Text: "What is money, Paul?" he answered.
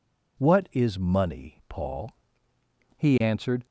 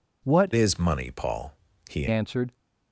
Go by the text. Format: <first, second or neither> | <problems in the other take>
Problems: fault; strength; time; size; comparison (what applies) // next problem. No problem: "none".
first | changes voice from "is" to "he"; from 0.5 to 2.0 s; 1.5 s long